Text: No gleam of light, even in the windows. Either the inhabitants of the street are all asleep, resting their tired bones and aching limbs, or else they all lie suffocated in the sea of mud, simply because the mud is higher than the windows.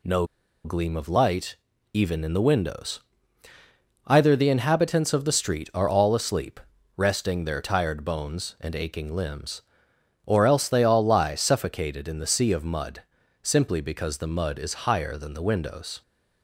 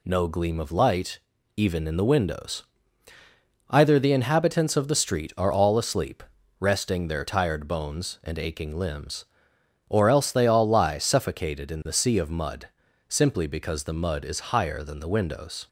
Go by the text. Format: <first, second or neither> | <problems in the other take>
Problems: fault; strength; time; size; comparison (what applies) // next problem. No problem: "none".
second | pauses between "No" and "gleam"; at 0.2 s; 0.38 s long